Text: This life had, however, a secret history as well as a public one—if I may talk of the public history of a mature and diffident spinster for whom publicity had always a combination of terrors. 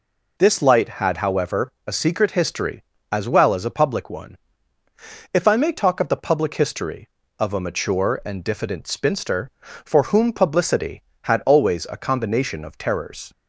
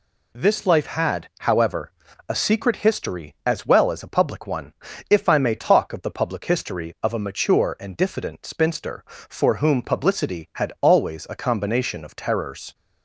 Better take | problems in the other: second | says "light" for "life"; at 0.6 s

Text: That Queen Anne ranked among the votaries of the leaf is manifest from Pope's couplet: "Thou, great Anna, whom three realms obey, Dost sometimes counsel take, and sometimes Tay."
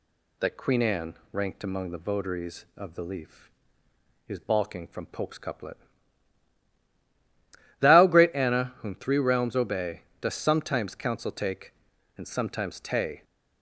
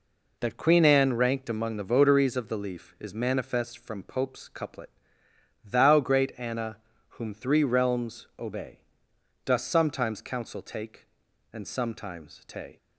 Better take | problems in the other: second | pauses between "Anne" and "ranked"; slight; at 1.1 s; 0.18 s long // says "balking" for "manifest"; at 4.3 s

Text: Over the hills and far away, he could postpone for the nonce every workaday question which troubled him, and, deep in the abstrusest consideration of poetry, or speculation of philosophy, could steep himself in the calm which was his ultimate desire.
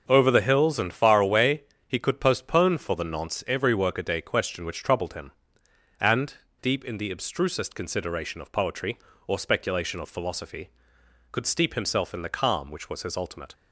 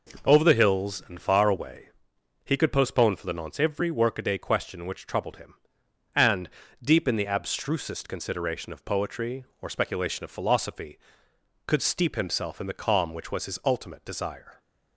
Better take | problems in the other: second | starts louder than the rest; until 1.0 s; 6.5 dB // stops before "desire"; at 13.5 s

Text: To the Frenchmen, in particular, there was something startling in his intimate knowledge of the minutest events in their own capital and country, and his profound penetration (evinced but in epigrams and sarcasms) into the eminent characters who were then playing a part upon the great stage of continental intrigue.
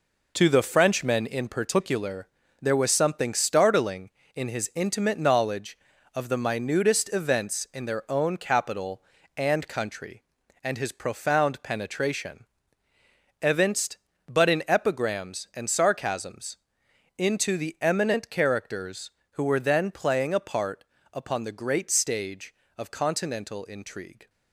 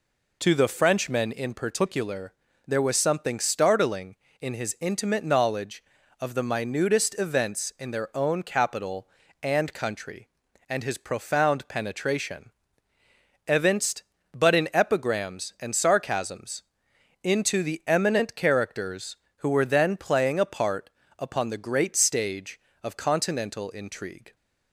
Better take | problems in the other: second | gets quieter; strong; throughout; 7.5 dB // pauses between "part" and "upon"; slight; at 20.8 s; 0.26 s long; slight in the second

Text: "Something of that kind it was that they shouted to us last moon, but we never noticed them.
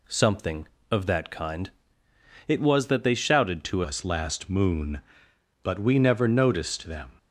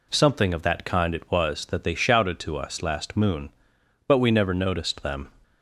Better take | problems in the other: second | pauses between "kind" and "it"; noticeable; at 1.7 s; 0.76 s long // changes voice at "us"; from 3.8 s on; 3.2 s long

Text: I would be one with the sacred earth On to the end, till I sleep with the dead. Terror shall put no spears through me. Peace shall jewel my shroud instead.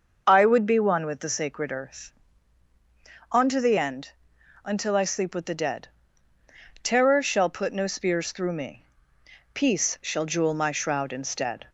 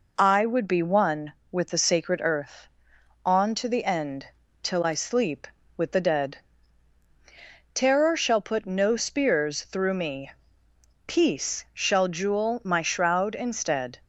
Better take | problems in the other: second | starts louder than the rest; noticeable; until 1.2 s; 6 dB // says "until" for "till"; at 4.6 s

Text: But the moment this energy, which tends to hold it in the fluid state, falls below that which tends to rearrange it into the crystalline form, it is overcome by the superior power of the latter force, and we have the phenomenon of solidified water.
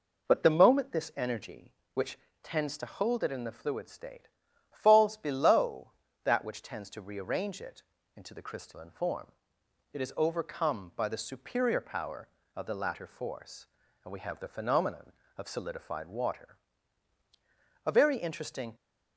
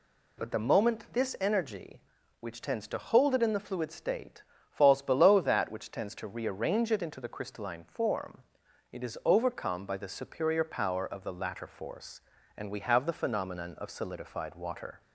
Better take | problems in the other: second | pauses between "which" and "tends"; slight; at 2.1 s; 0.26 s long // pauses between "it" and "into"; slight; at 7.8 s; 0.34 s long // goes on to say "A very interesting"; noticeable; from 17.8 s on; 0.90 s long

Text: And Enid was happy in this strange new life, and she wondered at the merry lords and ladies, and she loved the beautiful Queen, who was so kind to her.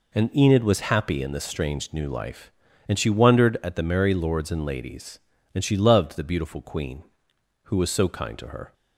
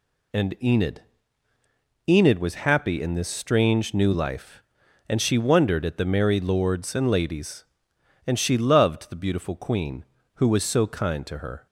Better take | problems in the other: first | says "Enid" twice; at 2.0 s

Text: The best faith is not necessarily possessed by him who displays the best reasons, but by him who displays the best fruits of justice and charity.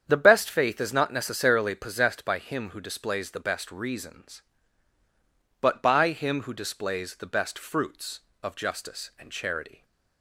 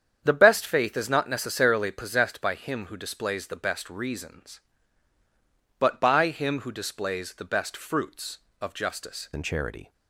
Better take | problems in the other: first | starts louder than the rest; strong; until 1.2 s; 8 dB; strong in the first // changes voice at "and"; from 9.3 s on; 0.6 s long

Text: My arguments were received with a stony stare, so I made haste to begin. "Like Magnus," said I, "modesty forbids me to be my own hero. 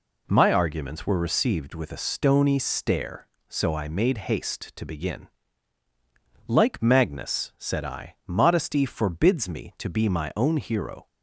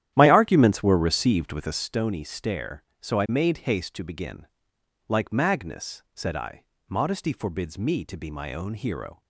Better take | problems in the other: first | starts louder than the rest; strong; until 1.9 s; 11.5 dB

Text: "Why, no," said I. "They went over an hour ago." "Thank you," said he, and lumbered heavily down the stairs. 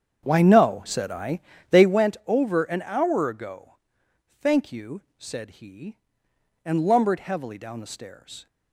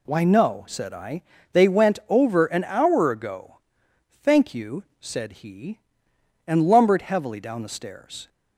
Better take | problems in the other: second | starts louder than the rest; strong; until 2.0 s; 8 dB

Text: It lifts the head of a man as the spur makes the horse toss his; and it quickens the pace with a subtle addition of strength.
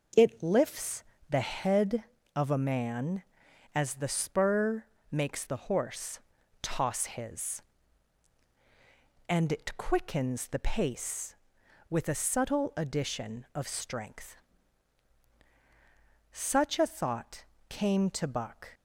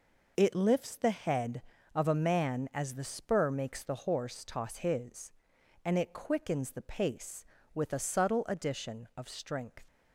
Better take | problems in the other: second | pauses between "lifts" and "the"; slight; at 1.0 s; 0.26 s long // pauses between "spur" and "makes"; slight; at 4.8 s; 0.26 s long // pauses between "horse" and "toss"; at 6.1 s; 0.42 s long // goes on to say "Such a thought came to Buck"; strong; from 16.3 s on; 2.4 s long

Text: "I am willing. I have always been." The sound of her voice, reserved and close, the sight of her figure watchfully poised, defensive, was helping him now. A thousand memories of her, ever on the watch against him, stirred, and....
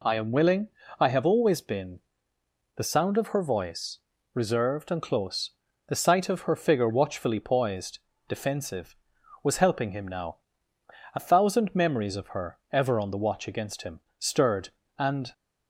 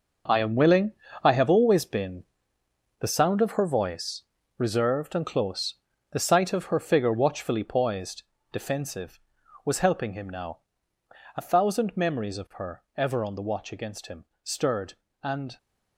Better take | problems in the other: first | gets quieter; strong; throughout; 11 dB

